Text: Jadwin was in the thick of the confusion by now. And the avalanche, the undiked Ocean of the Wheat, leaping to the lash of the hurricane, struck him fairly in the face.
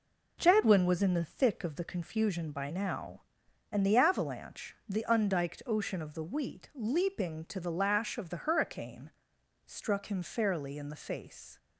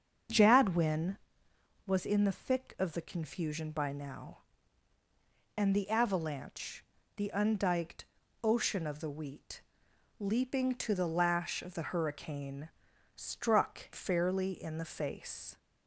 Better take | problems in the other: first | starts louder than the rest; until 2.0 s; 7 dB // pauses between "undiked" and "Ocean"; slight; at 8.0 s; 0.36 s long // skips "him"; at 13.9 s

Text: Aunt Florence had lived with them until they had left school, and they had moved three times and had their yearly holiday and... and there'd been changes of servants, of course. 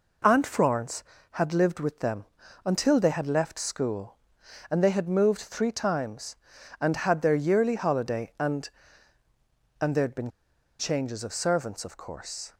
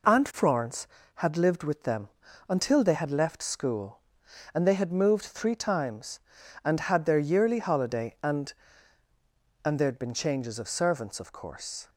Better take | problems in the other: second | pauses between "them" and "until"; at 2.2 s; 0.40 s long; also in the second // pauses between "been" and "changes"; noticeable; at 10.2 s; 0.50 s long

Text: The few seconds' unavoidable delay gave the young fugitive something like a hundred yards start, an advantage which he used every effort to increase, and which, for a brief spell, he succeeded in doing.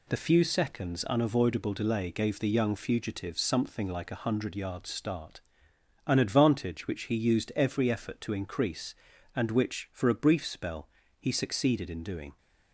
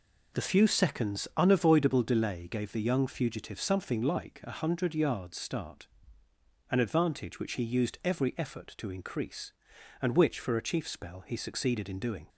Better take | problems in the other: first | says "chief" for "brief"; at 10.6 s

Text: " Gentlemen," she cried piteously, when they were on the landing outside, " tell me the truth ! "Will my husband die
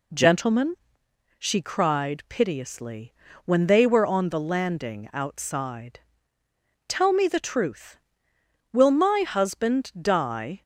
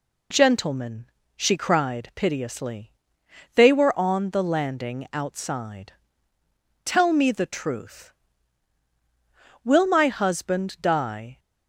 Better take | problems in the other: first | skips "when"; at 3.2 s

